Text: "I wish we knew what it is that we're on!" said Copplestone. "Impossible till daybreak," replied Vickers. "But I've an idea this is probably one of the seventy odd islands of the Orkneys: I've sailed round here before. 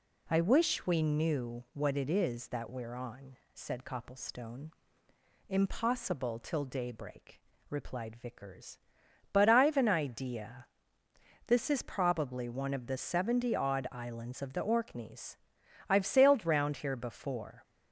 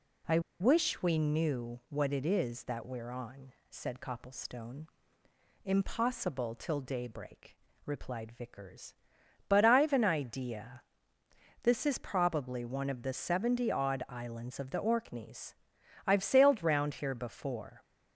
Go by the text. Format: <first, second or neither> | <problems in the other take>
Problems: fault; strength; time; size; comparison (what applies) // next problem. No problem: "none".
first | pauses between "I" and "wish"; slight; at 0.3 s; 0.20 s long // pauses between "idea" and "this"; noticeable; at 10.8 s; 0.80 s long; noticeable in the first